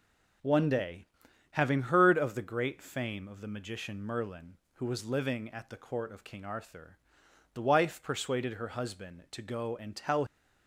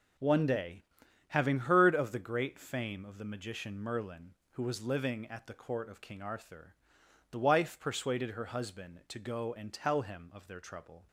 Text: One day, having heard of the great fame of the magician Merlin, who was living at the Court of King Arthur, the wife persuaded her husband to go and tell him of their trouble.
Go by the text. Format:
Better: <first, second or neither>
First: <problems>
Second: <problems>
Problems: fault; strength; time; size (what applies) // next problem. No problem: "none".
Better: second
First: stops before "him of their trouble"; at 10.2 s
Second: none